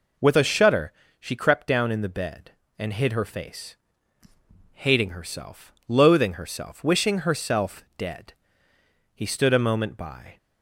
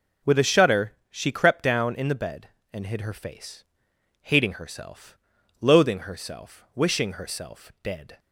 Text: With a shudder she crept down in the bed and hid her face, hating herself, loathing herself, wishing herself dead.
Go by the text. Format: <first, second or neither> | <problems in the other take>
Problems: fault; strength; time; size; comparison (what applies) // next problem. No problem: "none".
second | pauses between "shudder" and "she"; slight; at 0.9 s; 0.28 s long; slight in the second // goes on to say "He stood a moment by"; noticeable; from 9.1 s on; 1.2 s long